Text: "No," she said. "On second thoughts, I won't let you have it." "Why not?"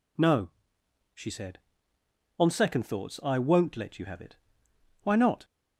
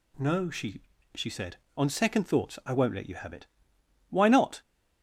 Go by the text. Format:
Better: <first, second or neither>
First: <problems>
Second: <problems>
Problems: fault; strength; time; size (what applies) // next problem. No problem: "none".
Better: first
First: none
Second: says "she" twice; at 1.1 s